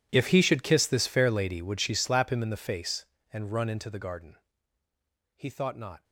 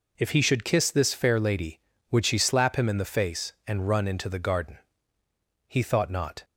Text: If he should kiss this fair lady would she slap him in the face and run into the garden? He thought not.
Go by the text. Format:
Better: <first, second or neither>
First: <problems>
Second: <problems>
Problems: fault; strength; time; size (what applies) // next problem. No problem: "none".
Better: second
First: gets quieter; strong; throughout; 21 dB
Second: none